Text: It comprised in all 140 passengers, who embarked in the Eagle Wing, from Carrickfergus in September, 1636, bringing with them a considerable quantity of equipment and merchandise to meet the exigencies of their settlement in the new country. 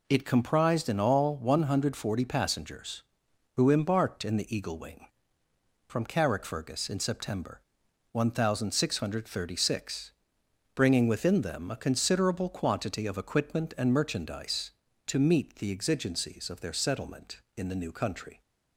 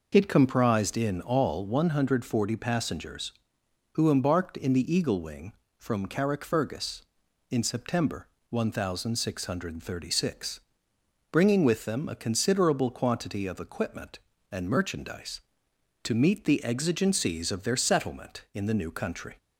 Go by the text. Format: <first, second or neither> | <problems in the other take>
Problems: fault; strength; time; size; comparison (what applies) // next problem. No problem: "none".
second | says "within" for "with"; at 11.0 s